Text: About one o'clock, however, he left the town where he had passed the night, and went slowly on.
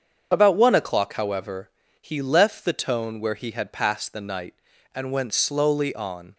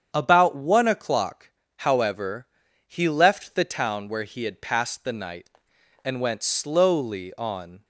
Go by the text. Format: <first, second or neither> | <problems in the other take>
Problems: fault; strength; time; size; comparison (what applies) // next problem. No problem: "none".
second | starts louder than the rest; strong; until 1.3 s; 7 dB; strong in the second // says "tone" for "town"; at 2.7 s